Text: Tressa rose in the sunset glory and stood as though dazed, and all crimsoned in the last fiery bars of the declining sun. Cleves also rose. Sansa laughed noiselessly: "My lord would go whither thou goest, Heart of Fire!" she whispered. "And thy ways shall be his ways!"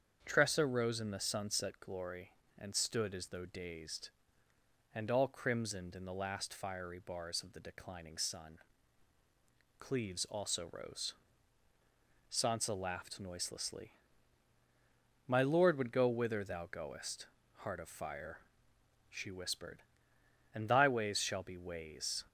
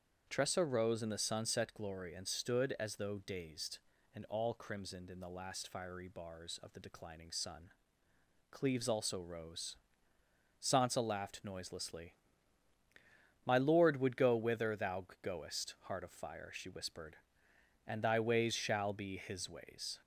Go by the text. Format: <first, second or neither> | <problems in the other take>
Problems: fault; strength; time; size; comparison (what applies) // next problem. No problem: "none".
second | starts louder than the rest; strong; until 1.2 s; 7.5 dB; strong in the second // skips "his"; at 21.5 s